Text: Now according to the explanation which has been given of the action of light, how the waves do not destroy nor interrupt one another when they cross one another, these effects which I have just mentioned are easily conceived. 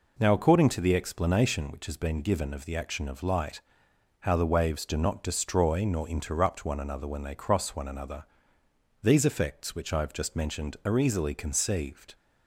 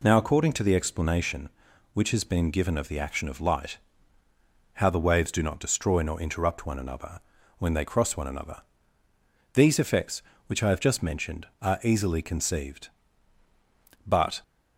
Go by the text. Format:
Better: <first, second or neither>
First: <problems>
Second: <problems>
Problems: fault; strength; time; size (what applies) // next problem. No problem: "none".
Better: first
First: none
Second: pauses between "another" and "when"; at 7.2 s; 0.38 s long // goes on to say "But"; slight; from 14.0 s on; 0.38 s long